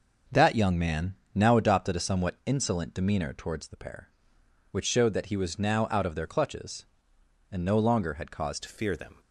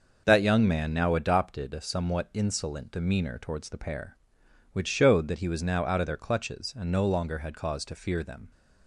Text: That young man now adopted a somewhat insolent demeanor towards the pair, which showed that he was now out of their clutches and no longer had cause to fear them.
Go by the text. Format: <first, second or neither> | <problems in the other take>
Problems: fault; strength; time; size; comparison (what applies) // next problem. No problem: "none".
second | starts louder than the rest; noticeable; until 1.5 s; 6 dB // pauses between "man" and "now"; slight; at 1.1 s; 0.18 s long // changes voice at "to"; from 8.6 s on; 0.5 s long